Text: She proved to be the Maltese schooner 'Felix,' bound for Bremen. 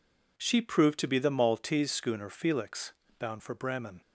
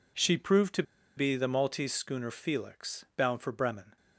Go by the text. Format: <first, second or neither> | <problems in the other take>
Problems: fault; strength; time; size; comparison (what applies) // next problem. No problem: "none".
first | pauses between "to" and "be"; slight; at 0.8 s; 0.34 s long